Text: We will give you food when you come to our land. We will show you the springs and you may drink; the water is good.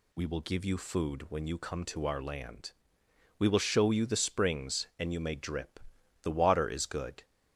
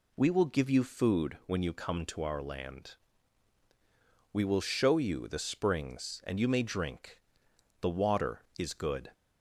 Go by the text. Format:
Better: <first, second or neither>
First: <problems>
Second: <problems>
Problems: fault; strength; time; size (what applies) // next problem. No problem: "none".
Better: second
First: says "drip" for "drink"; at 5.3 s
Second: none